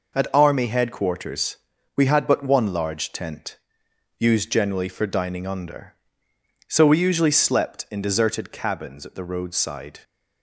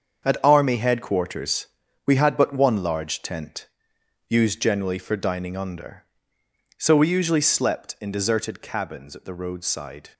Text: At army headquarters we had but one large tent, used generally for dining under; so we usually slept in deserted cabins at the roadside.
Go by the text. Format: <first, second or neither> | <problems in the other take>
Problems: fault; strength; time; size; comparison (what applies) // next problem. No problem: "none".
first | gets quieter; strong; throughout; 10 dB // pauses between "headquarters" and "we"; at 1.6 s; 0.40 s long; also in the first